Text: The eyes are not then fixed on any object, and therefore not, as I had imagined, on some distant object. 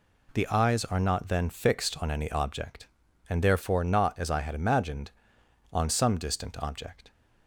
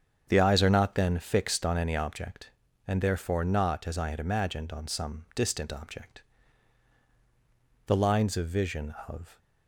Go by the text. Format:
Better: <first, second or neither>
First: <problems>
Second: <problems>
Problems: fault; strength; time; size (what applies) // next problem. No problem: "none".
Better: first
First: none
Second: starts louder than the rest; strong; until 1.2 s; 7.5 dB // goes on to say "The lines of vision of"; from 7.8 s on; 1.5 s long